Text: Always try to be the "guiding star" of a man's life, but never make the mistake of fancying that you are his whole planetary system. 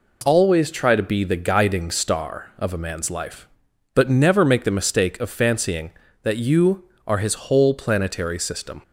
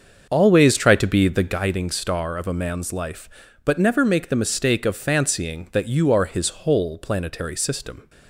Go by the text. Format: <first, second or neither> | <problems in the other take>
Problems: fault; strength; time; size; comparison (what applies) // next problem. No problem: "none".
first | starts louder than the rest; until 1.7 s; 6.5 dB